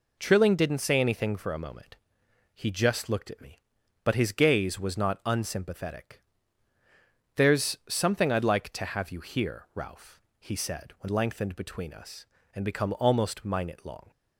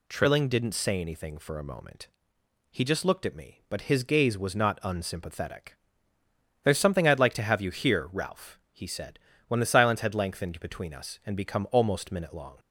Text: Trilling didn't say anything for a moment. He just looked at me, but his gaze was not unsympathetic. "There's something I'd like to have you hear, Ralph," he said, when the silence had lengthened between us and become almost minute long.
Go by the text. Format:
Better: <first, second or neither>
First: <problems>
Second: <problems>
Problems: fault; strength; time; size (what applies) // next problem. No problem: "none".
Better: second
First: skips "the silence had"; at 11.0 s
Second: none